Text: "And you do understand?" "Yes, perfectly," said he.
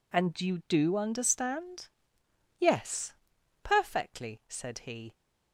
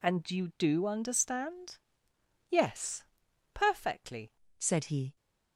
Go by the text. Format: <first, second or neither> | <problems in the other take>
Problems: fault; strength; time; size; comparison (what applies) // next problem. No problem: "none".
first | changes voice at "said"; from 4.5 s on; 0.6 s long